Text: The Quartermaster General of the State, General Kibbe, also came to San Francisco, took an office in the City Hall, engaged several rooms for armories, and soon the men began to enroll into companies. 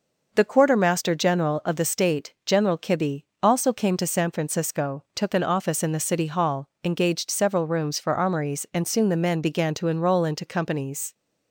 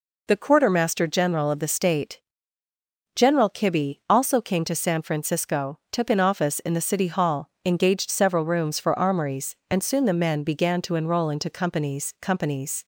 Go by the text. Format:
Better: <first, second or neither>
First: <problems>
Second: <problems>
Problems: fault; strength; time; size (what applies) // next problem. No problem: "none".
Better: first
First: none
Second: says "companies" twice; at 12.2 s